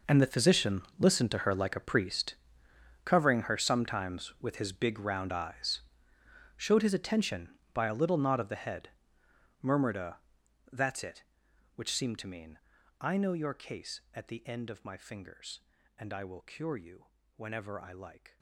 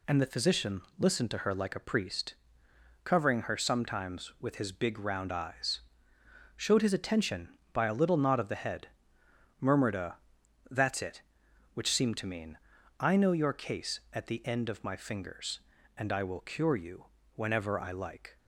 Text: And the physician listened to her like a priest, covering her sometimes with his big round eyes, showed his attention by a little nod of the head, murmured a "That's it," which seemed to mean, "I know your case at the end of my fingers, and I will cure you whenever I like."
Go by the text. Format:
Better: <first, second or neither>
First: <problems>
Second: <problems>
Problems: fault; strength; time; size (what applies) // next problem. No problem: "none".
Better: second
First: gets quieter; strong; throughout; 16.5 dB // pauses between "physician" and "listened"; slight; at 0.8 s; 0.16 s long // pauses between "a" and "That's"; noticeable; at 10.1 s; 0.52 s long // pauses between "you" and "whenever"; slight; at 17.0 s; 0.30 s long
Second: pauses between "physician" and "listened"; slight; at 0.8 s; 0.16 s long // pauses between "a" and "That's"; noticeable; at 10.1 s; 0.52 s long // pauses between "you" and "whenever"; slight; at 17.0 s; 0.30 s long